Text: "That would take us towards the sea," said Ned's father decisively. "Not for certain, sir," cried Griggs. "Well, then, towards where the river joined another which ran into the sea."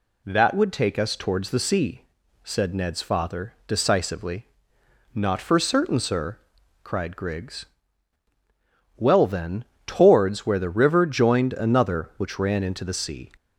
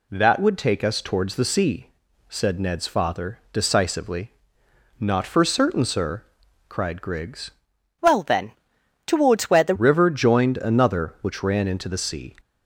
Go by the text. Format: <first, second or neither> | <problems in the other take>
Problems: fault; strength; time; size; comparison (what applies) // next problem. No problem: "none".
first | changes voice from "Well" to "the"; from 8.0 to 9.7 s; 1.7 s long